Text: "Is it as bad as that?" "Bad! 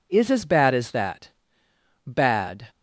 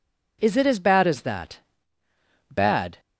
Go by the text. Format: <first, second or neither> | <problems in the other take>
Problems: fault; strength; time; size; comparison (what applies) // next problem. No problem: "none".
second | skips "it"; at 0.2 s